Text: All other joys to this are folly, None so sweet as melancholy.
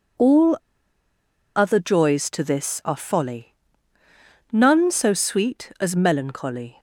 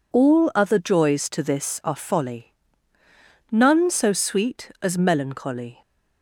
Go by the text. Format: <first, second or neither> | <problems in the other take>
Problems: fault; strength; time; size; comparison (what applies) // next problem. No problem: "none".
second | pauses between "All" and "other"; at 0.5 s; 0.99 s long